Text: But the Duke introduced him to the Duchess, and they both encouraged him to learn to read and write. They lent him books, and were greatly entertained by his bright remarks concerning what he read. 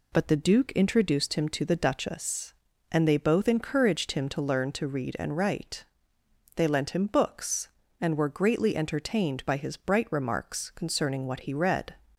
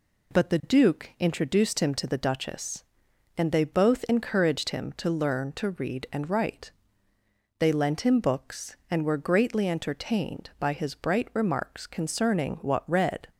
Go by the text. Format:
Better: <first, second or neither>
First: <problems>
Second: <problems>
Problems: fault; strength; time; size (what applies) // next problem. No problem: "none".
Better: first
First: none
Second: skips "he"; at 12.8 s